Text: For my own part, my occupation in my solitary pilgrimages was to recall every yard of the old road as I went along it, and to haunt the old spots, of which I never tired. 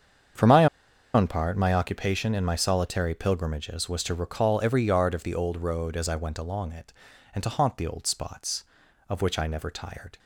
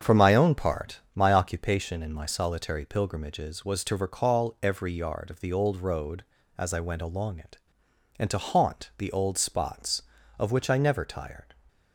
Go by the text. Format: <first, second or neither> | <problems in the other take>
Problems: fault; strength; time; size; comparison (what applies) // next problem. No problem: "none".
second | starts louder than the rest; strong; until 1.8 s; 7.5 dB; strong in the second // pauses between "my" and "own"; noticeable; at 0.6 s; 0.47 s long